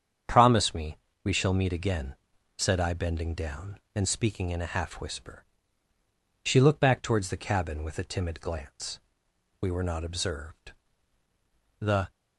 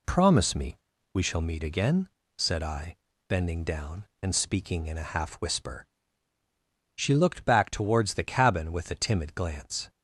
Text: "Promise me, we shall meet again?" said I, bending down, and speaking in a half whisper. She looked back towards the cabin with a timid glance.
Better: second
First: starts louder than the rest; strong; until 1.5 s; 8 dB // goes on to say "We were not observed The"; strong; from 9.6 s on; 2.5 s long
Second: none

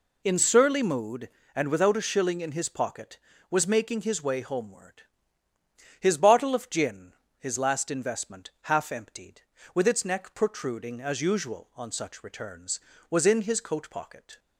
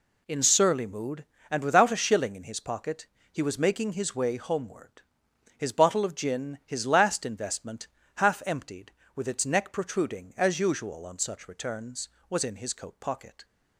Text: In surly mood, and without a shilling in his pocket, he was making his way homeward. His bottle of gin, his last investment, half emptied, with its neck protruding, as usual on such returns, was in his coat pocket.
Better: second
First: skips "he"; at 3.3 s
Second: none

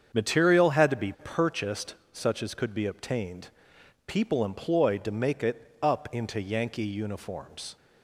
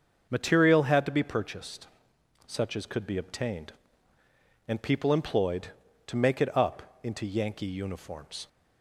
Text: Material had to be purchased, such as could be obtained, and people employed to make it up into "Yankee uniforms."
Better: second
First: starts louder than the rest; strong; until 1.2 s; 7.5 dB // skips "and"; at 3.7 s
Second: starts louder than the rest; until 1.3 s; 6.5 dB

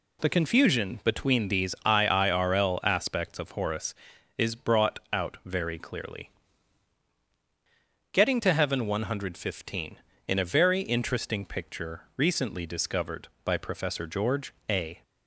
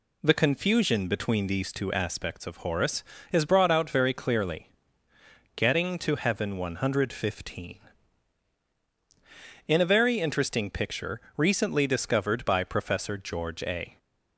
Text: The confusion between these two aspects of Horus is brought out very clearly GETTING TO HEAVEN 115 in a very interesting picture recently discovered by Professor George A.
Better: second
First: says "iirl" for "two"; at 1.8 s // pauses between "brought" and "out"; slight; at 4.9 s; 0.16 s long // pauses between "clearly" and "GETTING"; strong; at 6.3 s; 1.8 s long // pauses between "picture" and "recently"; slight; at 12.0 s; 0.16 s long // pauses between "George" and "A"; slight; at 14.5 s; 0.16 s long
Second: pauses between "clearly" and "GETTING"; noticeable; at 4.6 s; 0.88 s long // pauses between "picture" and "recently"; slight; at 11.2 s; 0.18 s long

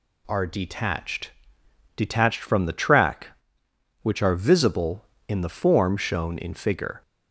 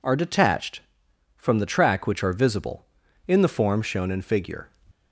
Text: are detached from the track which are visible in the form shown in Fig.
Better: second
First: says "detached" twice; at 1.9 s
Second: none

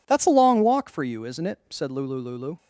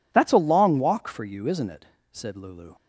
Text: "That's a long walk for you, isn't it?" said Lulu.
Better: second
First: says "Lulu" twice; at 2.1 s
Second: none

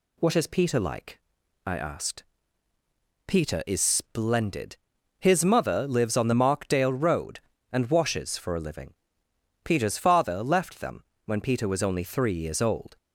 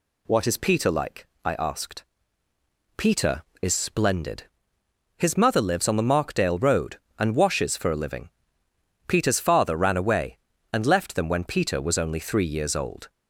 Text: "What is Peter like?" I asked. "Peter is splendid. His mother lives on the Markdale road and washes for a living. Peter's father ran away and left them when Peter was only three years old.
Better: second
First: skips "ran away and"; at 10.4 s // pauses between "them" and "when"; slight; at 11.0 s; 0.22 s long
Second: none

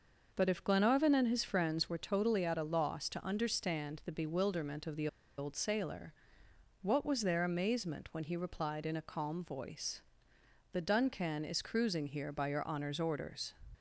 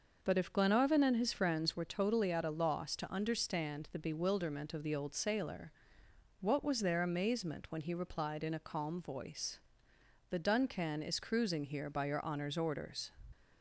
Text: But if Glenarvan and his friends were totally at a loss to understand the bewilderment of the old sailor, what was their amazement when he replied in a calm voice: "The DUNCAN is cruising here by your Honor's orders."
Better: second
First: pauses between "the" and "old"; slight; at 5.0 s; 0.31 s long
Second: none

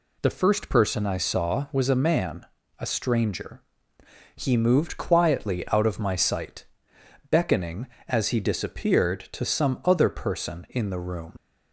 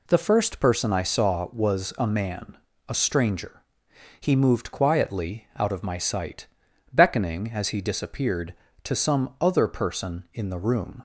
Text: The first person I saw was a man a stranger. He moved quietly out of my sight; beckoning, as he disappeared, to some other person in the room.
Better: second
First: pauses between "man" and "a"; slight; at 2.4 s; 0.36 s long // leaves "room" unfinished; at 11.3 s; 70 ms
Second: pauses between "man" and "a"; slight; at 2.5 s; 0.30 s long

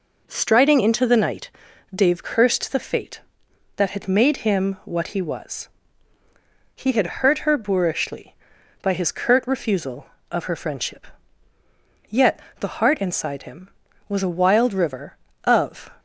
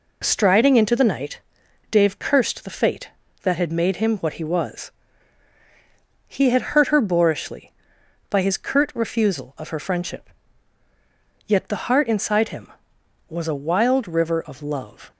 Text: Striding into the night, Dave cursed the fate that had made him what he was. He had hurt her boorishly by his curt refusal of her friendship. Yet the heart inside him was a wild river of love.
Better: second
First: pauses between "Yet" and "the"; slight; at 12.3 s; 0.20 s long // stops before "love"; at 15.9 s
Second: none

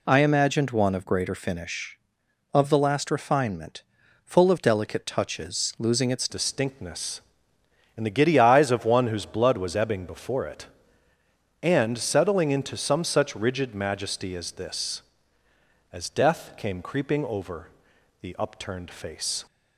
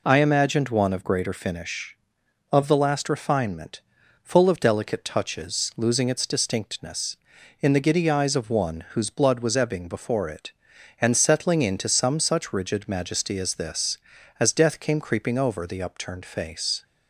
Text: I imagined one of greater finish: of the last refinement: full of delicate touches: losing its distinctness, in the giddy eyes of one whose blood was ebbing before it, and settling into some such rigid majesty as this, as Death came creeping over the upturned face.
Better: second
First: changes voice at "distinctness"; from 6.2 s on; 13.2 s long // pauses between "over" and "the"; noticeable; at 17.6 s; 0.52 s long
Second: none

